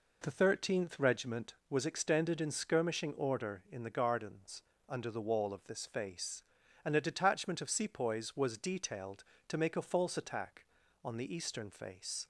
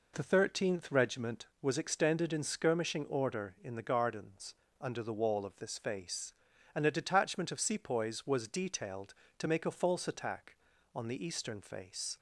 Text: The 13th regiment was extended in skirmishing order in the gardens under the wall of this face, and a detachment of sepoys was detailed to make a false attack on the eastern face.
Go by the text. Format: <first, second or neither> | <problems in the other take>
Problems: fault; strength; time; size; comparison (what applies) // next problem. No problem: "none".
neither | pauses between "gardens" and "under"; slight; the same in both